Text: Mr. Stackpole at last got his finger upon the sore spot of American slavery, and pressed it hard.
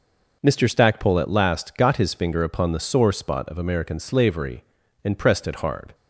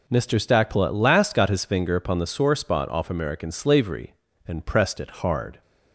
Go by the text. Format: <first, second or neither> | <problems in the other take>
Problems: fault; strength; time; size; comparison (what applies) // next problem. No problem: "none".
first | says "off" for "of"; at 2.8 s